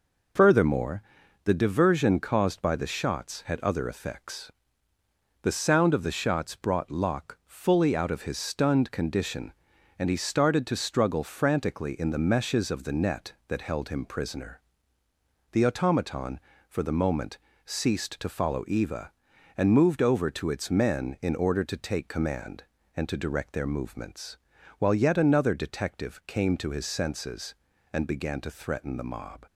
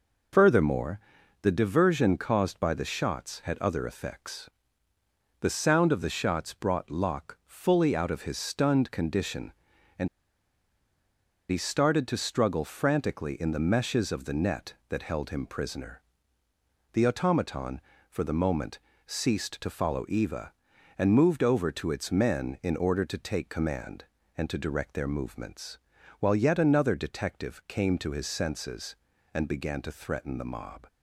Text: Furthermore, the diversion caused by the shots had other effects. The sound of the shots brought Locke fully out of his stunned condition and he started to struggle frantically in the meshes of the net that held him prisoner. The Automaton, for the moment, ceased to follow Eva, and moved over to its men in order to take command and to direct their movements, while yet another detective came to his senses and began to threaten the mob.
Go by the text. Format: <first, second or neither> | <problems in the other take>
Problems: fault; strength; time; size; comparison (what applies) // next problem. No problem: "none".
first | pauses between "and" and "he"; strong; at 10.0 s; 1.4 s long